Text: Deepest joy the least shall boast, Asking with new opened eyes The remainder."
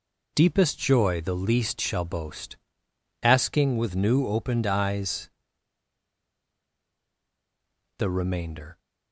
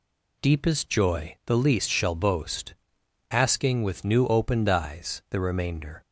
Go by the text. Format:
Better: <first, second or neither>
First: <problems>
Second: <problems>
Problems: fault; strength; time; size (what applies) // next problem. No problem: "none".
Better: second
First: pauses between "eyes" and "The"; strong; at 5.3 s; 2.6 s long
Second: none